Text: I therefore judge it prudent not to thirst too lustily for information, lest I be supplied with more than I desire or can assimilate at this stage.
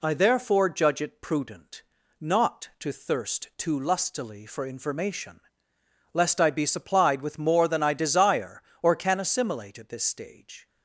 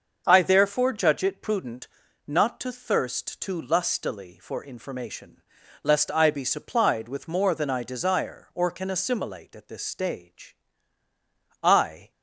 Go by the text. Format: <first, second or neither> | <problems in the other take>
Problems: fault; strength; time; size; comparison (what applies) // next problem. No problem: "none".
first | starts louder than the rest; until 1.2 s; 6.5 dB // pauses between "prudent" and "not"; at 1.8 s; 0.40 s long; slight in the first // goes on to say "I"; slight; from 11.6 s on; 0.48 s long